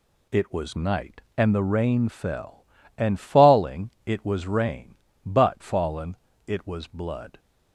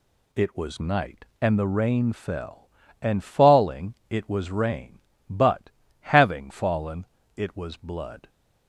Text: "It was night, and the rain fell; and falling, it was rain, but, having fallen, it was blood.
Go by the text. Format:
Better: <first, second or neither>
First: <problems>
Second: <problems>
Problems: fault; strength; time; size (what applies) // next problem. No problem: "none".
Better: second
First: skips "having"; at 5.6 s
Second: none